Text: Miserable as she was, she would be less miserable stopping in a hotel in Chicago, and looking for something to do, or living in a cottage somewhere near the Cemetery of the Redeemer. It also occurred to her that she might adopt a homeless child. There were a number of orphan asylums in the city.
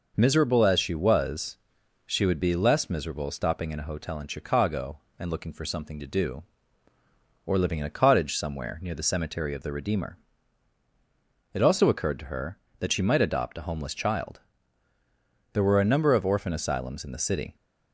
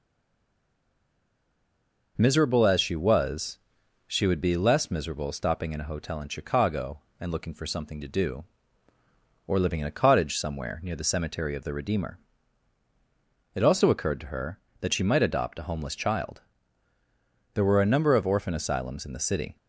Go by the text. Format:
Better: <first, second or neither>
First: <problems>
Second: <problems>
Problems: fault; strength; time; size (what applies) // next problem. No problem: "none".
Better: first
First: none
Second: stays silent before the first word; until 2.1 s; 2.1 s long